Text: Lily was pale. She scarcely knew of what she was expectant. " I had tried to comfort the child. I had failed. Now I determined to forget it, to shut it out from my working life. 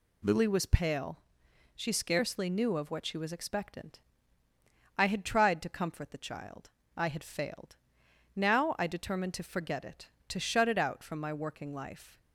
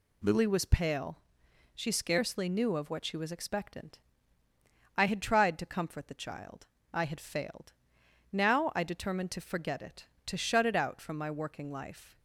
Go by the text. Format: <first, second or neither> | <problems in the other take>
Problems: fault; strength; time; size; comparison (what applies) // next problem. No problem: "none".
neither | none